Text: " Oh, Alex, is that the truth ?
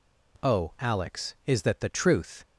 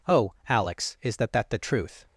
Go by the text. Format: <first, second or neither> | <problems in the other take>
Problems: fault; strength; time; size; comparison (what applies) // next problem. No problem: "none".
first | says "that" twice; at 1.3 s